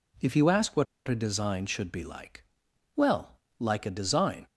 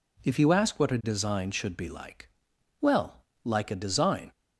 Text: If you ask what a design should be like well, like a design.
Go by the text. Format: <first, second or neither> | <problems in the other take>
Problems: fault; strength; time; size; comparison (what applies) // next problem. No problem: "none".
second | pauses between "what" and "a"; slight; at 0.8 s; 0.22 s long // pauses between "like" and "well"; noticeable; at 2.4 s; 0.52 s long; noticeable in the second